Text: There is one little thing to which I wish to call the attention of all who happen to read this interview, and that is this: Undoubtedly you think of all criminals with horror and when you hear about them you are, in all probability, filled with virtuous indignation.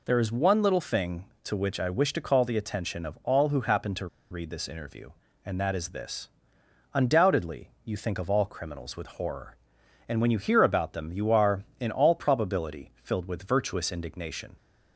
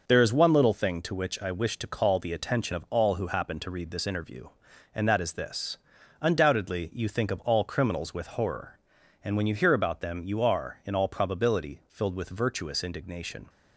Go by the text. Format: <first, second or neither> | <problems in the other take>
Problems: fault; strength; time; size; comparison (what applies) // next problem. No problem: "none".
second | pauses between "to" and "read"; slight; at 4.0 s; 0.23 s long